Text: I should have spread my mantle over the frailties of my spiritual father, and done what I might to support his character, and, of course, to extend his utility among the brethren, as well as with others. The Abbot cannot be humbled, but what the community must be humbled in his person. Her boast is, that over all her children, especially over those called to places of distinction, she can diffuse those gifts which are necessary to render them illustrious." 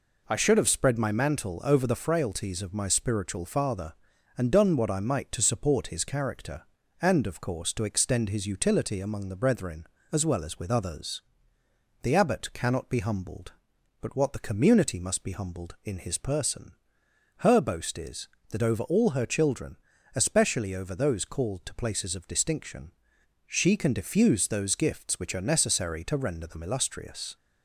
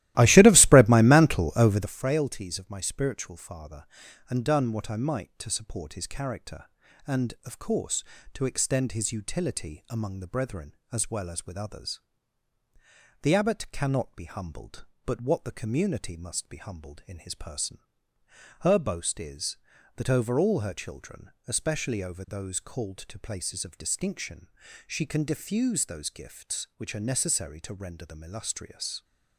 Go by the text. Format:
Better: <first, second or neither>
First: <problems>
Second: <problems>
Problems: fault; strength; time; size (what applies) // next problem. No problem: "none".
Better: first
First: none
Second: starts louder than the rest; strong; until 2.0 s; 16 dB